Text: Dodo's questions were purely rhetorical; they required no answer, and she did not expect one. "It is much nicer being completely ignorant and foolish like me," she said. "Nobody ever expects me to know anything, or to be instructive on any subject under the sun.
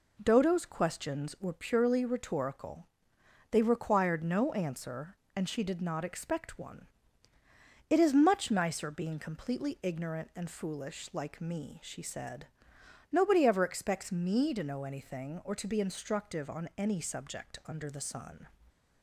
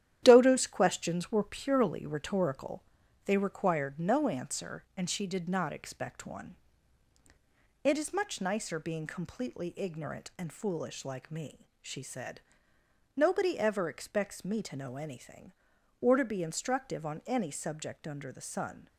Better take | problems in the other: first | gets quieter; throughout; 6.5 dB

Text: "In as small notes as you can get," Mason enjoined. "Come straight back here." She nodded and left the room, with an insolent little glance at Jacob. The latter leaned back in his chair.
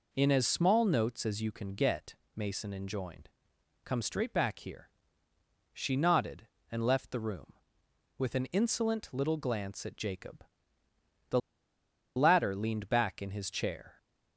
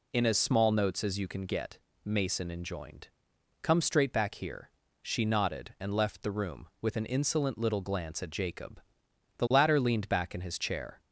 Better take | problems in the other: second | pauses between "The" and "latter"; noticeable; at 11.3 s; 0.76 s long

